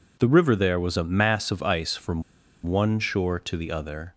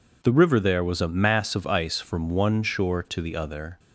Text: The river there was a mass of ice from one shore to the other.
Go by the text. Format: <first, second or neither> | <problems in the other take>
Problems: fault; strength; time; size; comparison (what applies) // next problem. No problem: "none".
second | pauses between "from" and "one"; at 2.2 s; 0.43 s long